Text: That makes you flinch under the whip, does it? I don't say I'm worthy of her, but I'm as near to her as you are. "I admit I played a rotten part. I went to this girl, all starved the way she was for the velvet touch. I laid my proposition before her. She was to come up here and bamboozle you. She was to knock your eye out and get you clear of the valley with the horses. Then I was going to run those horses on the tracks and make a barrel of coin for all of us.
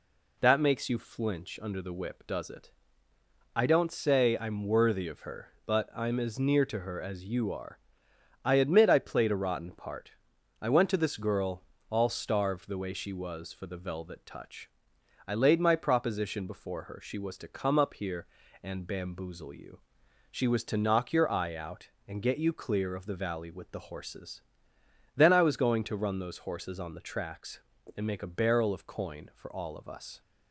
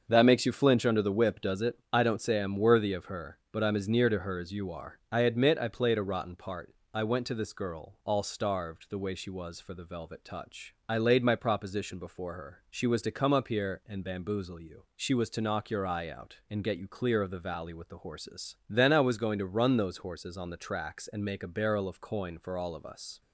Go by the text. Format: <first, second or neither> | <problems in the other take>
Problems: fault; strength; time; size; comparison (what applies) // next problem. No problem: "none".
first | starts louder than the rest; until 1.7 s; 6.5 dB